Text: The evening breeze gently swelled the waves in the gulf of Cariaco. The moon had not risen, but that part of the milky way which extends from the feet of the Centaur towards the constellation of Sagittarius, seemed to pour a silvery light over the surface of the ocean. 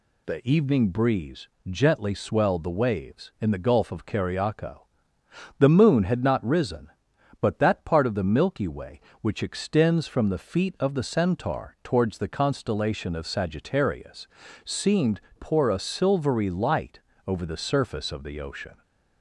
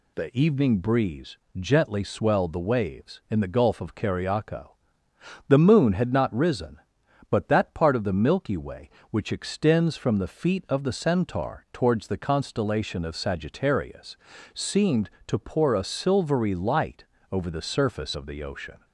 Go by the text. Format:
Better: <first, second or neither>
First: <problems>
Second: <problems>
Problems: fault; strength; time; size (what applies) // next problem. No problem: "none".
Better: second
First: pauses between "breeze" and "gently"; slight; at 1.4 s; 0.20 s long // skips "to"; at 15.2 s // pauses between "light" and "over"; slight; at 17.0 s; 0.26 s long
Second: pauses between "breeze" and "gently"; slight; at 1.3 s; 0.20 s long // pauses between "light" and "over"; slight; at 17.0 s; 0.26 s long